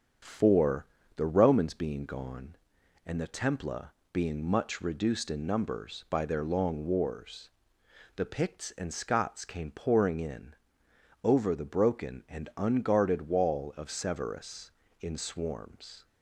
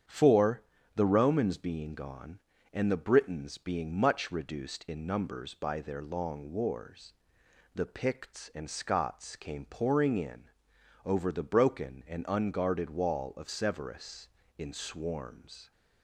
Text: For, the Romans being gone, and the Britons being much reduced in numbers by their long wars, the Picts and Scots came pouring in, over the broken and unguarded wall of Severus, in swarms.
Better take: second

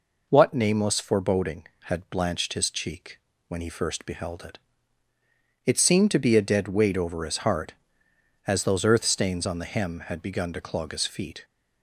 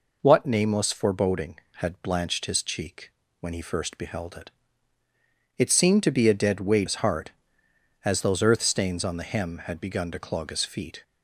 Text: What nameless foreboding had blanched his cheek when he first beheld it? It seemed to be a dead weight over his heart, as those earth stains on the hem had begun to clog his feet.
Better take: first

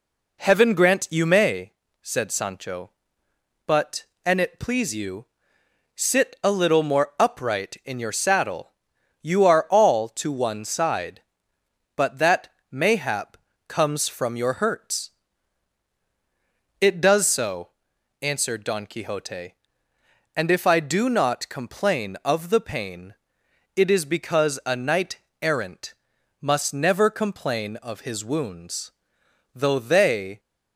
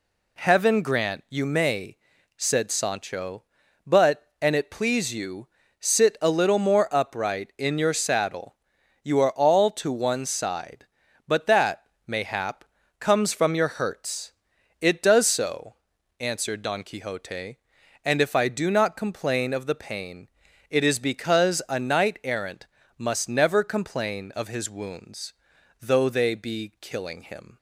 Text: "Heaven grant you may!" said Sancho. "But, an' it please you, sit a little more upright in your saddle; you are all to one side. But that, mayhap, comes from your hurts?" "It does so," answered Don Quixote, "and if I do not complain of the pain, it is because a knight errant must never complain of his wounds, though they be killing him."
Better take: second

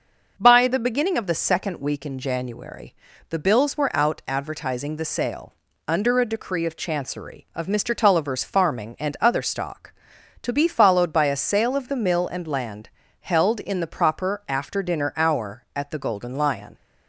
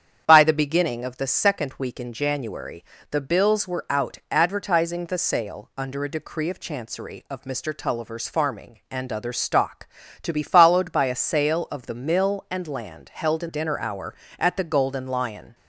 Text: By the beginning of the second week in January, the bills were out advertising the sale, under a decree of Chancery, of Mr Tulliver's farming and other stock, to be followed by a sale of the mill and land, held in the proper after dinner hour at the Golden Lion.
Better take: first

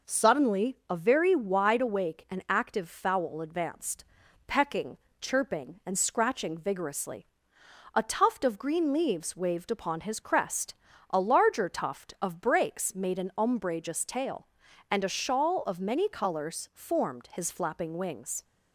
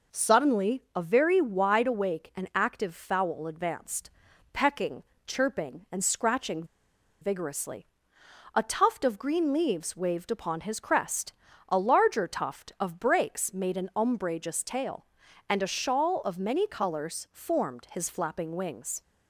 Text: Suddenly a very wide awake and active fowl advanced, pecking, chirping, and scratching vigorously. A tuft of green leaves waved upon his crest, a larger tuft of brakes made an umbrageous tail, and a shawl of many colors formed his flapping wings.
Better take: first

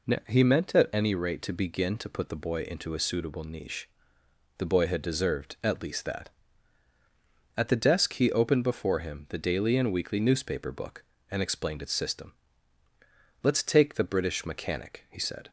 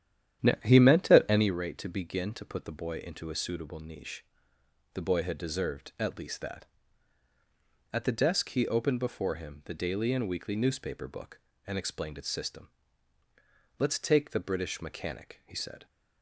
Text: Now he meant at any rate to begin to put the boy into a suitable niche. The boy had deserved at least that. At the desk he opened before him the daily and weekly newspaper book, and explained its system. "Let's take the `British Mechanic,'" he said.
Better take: first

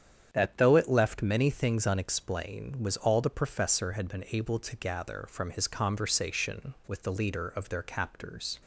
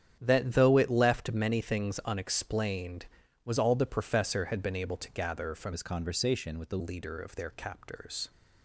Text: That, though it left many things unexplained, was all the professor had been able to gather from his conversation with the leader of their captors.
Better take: first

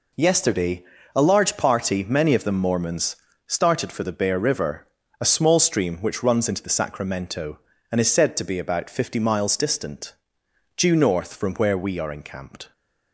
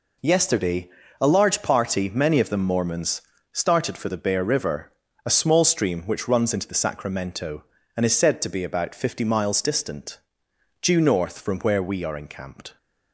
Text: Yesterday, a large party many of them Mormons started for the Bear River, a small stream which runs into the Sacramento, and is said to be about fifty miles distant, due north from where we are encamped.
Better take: neither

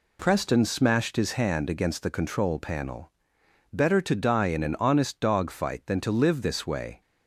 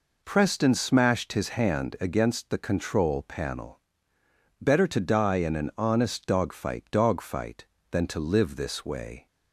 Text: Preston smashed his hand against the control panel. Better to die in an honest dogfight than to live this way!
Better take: first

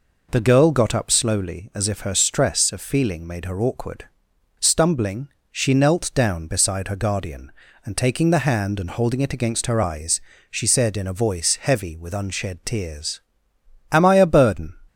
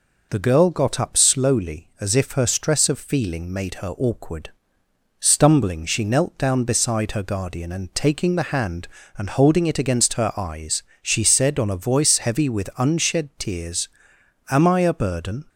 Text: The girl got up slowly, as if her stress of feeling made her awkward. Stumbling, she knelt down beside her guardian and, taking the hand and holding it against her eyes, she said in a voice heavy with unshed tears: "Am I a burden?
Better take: first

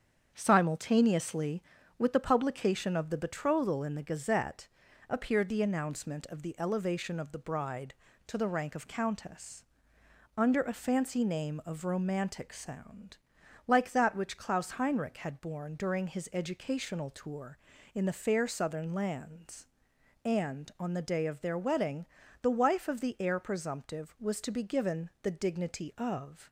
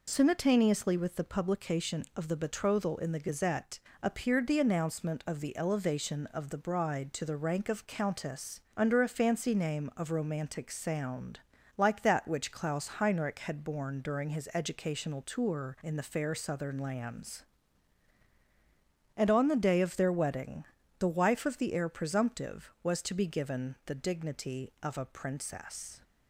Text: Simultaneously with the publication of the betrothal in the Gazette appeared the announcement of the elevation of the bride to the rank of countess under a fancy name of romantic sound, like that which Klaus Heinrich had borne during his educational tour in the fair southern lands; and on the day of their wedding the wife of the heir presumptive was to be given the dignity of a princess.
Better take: second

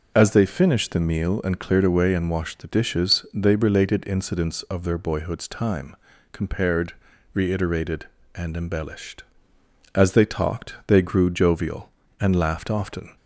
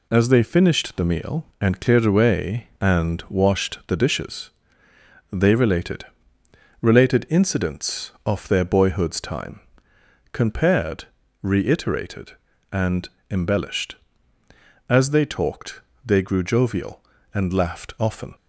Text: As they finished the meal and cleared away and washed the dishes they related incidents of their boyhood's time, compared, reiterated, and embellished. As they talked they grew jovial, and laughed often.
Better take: first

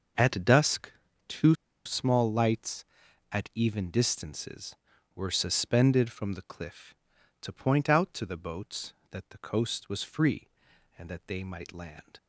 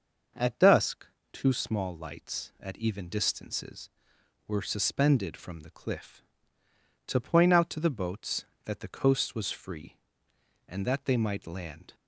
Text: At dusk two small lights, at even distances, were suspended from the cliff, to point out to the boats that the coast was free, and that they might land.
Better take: second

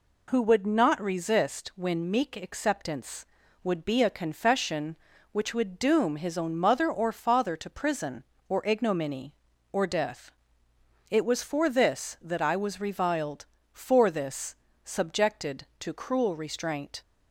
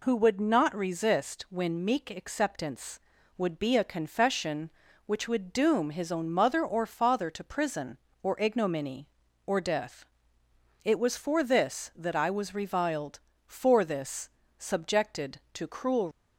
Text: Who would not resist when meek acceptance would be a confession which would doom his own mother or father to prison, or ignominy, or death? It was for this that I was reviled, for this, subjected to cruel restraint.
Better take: first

